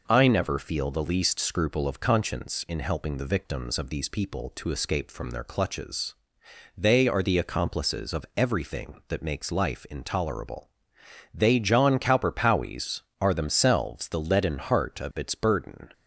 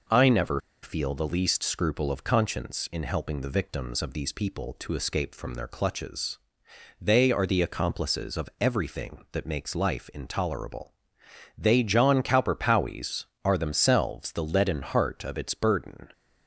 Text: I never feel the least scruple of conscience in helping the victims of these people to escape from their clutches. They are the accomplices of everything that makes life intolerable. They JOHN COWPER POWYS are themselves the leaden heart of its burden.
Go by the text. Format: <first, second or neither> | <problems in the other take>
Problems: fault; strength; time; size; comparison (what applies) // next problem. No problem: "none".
first | pauses between "never" and "feel"; slight; at 0.6 s; 0.22 s long